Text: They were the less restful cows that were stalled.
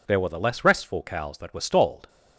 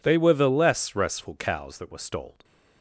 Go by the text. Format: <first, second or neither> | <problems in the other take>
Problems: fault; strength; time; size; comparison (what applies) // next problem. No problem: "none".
second | says "There" for "They"; at 0.0 s